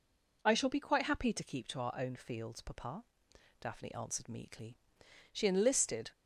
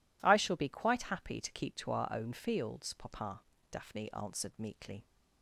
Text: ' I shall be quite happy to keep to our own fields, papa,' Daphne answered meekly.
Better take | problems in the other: second | goes on to say "She enlisted"; noticeable; from 5.3 s on; 0.78 s long

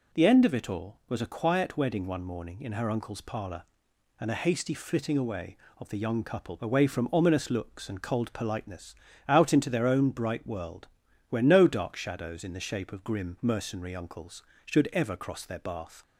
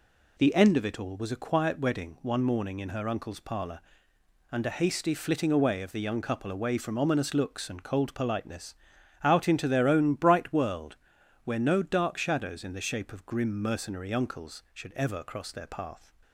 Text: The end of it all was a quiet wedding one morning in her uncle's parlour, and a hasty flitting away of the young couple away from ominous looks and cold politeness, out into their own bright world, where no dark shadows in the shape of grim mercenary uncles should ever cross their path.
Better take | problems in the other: second | says "bath" for "path"; at 15.5 s

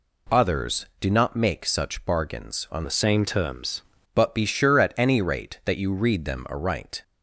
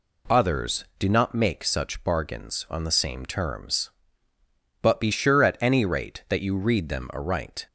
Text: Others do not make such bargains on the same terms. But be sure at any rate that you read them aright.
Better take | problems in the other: second | changes voice from "the" to "terms"; from 2.8 to 3.8 s; 1.0 s long

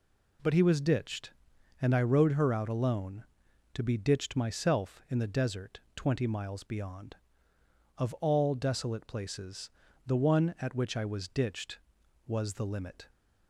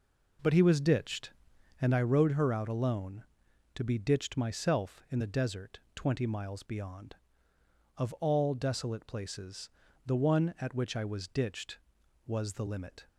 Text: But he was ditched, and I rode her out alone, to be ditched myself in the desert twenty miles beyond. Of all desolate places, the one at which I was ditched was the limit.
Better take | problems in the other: first | starts louder than the rest; noticeable; until 1.9 s; 4.5 dB // pauses between "desert" and "twenty"; slight; at 5.7 s; 0.16 s long; slight in the first

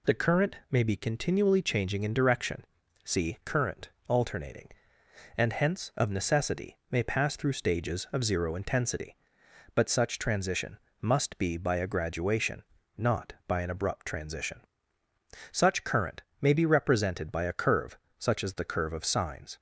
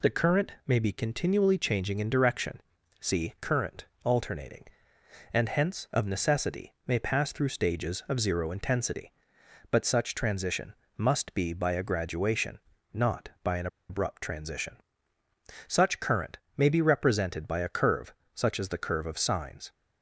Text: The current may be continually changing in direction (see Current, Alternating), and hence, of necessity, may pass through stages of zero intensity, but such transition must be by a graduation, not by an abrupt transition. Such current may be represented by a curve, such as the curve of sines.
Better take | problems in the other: first | pauses between "transition" and "must"; slight; at 10.7 s; 0.24 s long; slight in the first // pauses between "an" and "abrupt"; slight; at 13.6 s; 0.22 s long // pauses between "current" and "may"; slight; at 16.3 s; 0.18 s long; slight in the first

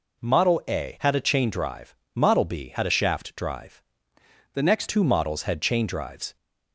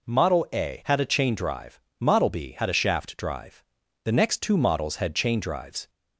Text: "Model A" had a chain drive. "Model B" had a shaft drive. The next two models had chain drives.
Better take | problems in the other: second | changes voice from "The" to "next"; from 4.5 to 4.8 s; 0.3 s long

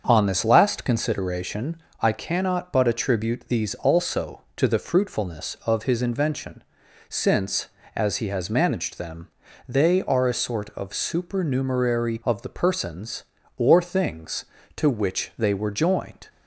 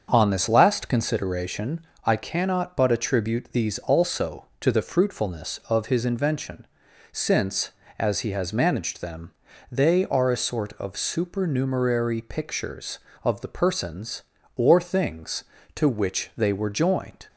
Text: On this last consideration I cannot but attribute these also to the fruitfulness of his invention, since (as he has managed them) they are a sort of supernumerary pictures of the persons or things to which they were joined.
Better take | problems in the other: second | starts louder than the rest; until 1.0 s; 7 dB; also in the second // pauses between "consideration" and "I"; slight; at 1.8 s; 0.18 s long; slight in the second // skips "pictures"; at 12.2 s

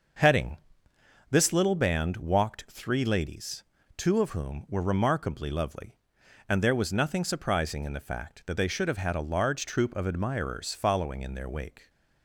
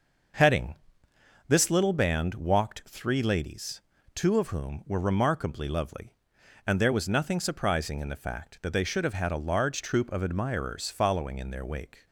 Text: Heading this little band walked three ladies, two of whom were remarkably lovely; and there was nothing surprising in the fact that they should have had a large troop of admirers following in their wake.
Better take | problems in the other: neither | starts louder than the rest; the same in both // pauses between "Heading" and "this"; noticeable; the same in both

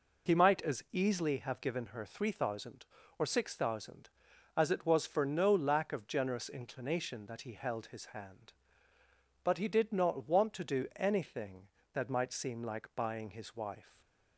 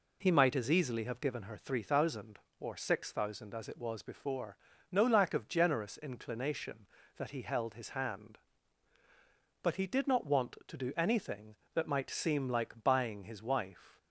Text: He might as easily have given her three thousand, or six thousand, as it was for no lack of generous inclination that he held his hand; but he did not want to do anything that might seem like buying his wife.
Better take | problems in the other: first | says "before" for "for"; at 4.0 s

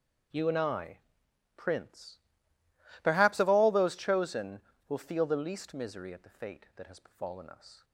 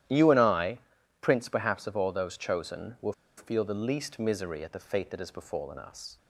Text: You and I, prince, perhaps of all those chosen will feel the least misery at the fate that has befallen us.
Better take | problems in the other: first | starts louder than the rest; strong; until 1.5 s; 12 dB; also in the first // pauses between "will" and "feel"; slight; at 3.1 s; 0.25 s long

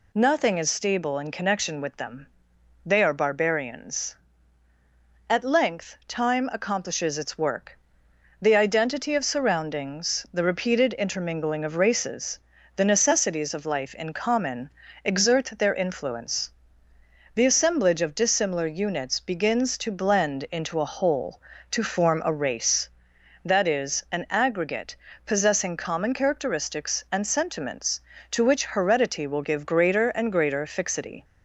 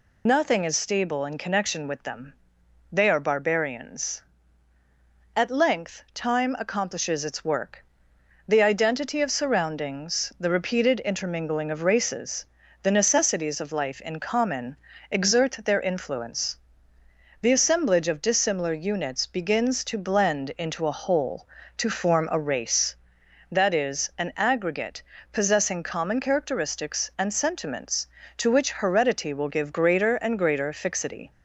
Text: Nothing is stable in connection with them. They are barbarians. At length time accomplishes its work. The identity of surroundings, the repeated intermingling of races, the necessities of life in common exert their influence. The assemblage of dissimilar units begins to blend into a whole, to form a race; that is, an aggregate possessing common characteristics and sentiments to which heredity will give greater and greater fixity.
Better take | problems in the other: first | loses the start of "Nothing"; at 0.2 s; 45 ms // pauses between "common" and "exert"; slight; at 14.7 s; 0.34 s long; slight in the first // pauses between "aggregate" and "possessing"; slight; at 25.0 s; 0.28 s long; slight in the first

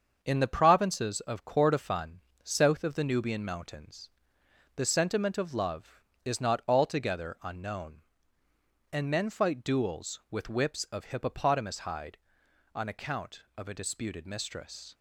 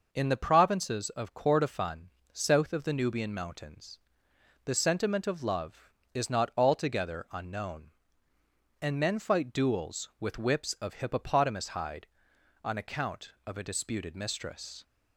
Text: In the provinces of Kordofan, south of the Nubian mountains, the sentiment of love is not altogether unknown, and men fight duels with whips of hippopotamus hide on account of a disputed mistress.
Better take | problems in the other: second | gets quieter; noticeable; throughout; 5 dB

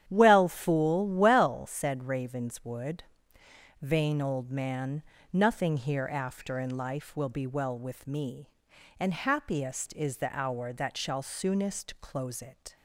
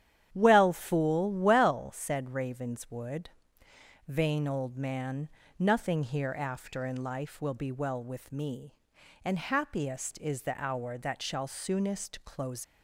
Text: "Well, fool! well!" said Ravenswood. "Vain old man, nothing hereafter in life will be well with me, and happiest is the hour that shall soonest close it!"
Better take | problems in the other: first | starts louder than the rest; strong; until 1.3 s; 10 dB; strong in the first // stops before "it"; at 12.6 s

